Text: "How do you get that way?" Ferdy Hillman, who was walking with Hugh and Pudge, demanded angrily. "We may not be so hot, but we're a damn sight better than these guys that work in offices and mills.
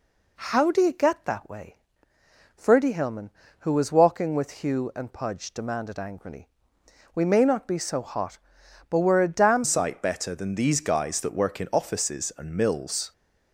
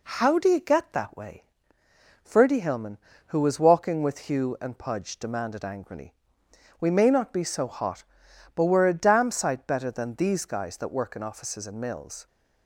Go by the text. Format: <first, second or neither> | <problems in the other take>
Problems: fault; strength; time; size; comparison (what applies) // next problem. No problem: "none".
second | changes voice at "sight"; from 9.6 s on; 3.5 s long